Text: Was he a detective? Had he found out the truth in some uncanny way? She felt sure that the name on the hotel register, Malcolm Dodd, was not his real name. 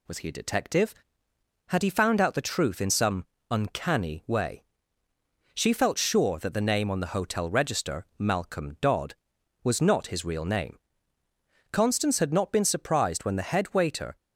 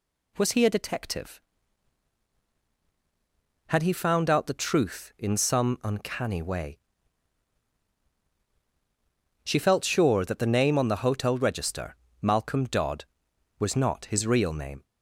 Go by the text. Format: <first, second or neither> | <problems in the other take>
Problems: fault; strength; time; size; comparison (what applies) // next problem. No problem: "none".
second | pauses between "some" and "uncanny"; slight; at 3.2 s; 0.26 s long // goes on to say "Constance had not been surprised when the head waiter"; strong; from 11.7 s on; 2.4 s long